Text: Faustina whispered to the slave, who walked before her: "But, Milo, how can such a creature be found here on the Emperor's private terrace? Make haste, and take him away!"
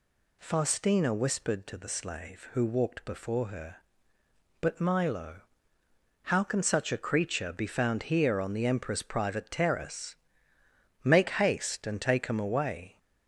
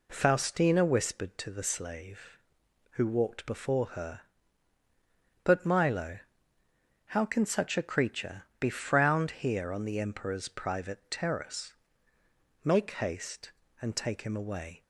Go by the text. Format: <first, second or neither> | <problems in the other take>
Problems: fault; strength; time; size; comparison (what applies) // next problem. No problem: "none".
first | pauses between "creature" and "be"; slight; at 8.4 s; 0.16 s long // says "frowned" for "found"; at 8.6 s